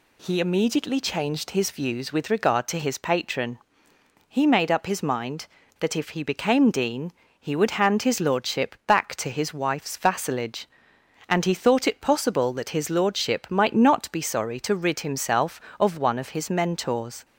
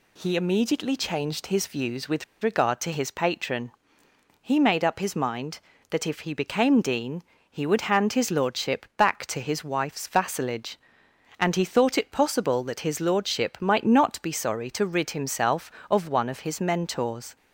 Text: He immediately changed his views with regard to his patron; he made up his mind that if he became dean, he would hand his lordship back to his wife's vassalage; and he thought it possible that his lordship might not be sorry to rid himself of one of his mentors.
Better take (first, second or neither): first